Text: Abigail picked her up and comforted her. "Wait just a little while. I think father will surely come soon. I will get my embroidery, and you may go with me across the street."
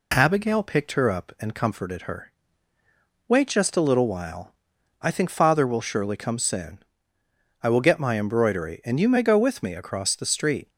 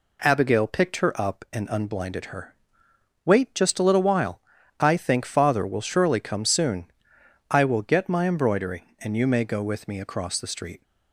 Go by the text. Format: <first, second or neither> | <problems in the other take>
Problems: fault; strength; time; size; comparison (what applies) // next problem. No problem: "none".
first | says "unblinded" for "comforted"; at 1.7 s